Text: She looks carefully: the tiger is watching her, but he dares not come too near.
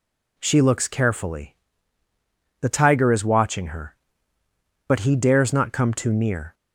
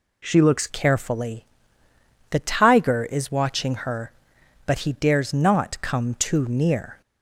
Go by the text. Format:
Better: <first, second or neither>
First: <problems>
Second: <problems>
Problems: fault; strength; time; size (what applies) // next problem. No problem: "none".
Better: first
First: none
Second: changes voice at "carefully"; from 0.6 s on; 6.4 s long